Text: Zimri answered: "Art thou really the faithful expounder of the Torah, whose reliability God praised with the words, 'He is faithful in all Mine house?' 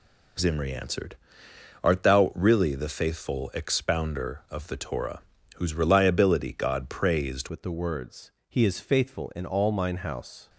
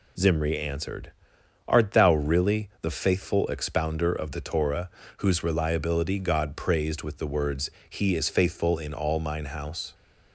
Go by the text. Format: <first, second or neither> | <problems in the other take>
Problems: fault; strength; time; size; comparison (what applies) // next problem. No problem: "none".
second | changes voice at "with"; from 7.4 s on; 3.0 s long